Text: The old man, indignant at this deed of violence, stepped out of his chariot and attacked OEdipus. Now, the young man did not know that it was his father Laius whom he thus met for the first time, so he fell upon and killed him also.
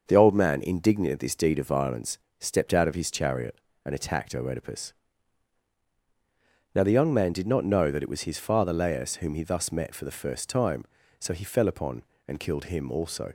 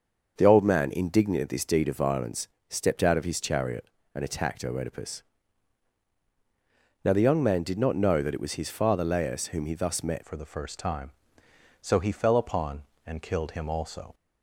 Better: first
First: starts louder than the rest; until 1.0 s; 6.5 dB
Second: starts louder than the rest; until 1.3 s; 6.5 dB // changes voice at "for"; from 10.2 s on; 3.9 s long

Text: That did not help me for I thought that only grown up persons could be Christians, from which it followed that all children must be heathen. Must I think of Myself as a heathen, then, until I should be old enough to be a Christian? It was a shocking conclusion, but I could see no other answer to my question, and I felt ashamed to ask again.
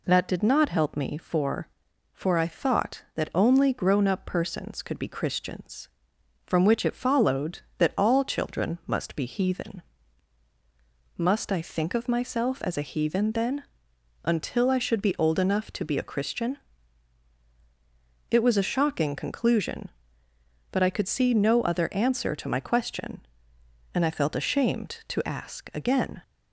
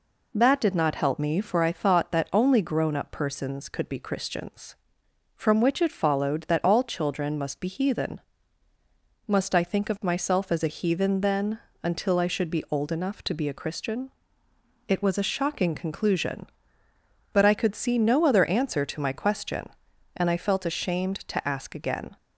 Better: second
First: says "for" twice; at 2.1 s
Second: none

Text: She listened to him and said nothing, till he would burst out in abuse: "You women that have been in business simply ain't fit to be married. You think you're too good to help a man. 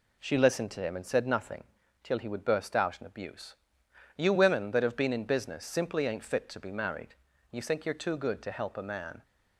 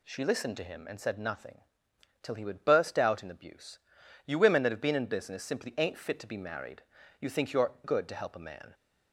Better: first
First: none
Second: skips "too"; at 7.7 s

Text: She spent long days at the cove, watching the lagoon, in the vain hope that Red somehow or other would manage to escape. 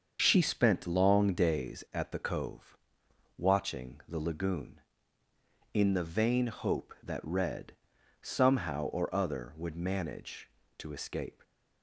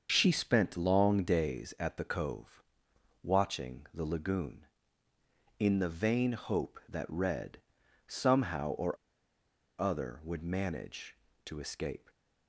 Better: first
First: starts louder than the rest; until 1.2 s; 7 dB // pauses between "Red" and "somehow"; noticeable; at 7.7 s; 0.50 s long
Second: starts louder than the rest; until 1.1 s; 7 dB // pauses between "Red" and "somehow"; noticeable; at 7.5 s; 0.50 s long // pauses between "or" and "other"; noticeable; at 8.9 s; 0.83 s long

